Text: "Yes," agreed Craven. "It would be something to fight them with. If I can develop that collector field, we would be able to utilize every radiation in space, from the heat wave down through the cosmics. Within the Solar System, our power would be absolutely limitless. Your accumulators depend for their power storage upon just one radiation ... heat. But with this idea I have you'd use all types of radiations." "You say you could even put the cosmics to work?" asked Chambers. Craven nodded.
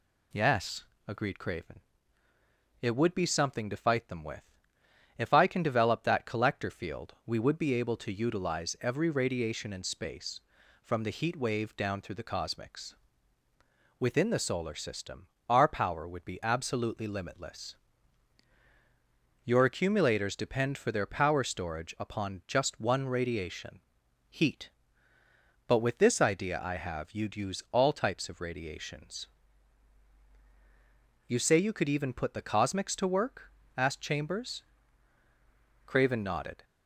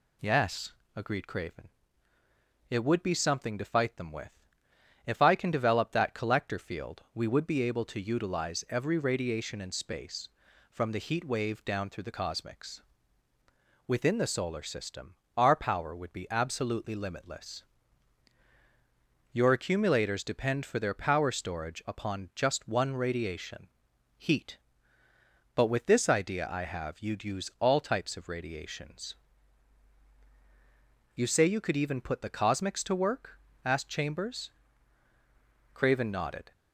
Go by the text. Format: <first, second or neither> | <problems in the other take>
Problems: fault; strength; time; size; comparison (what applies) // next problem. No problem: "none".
neither | none